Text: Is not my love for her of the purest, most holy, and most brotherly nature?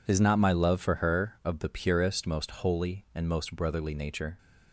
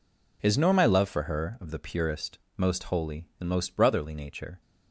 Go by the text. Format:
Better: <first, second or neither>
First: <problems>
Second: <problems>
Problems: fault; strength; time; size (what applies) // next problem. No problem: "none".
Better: first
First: none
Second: says "nor" for "not"; at 0.5 s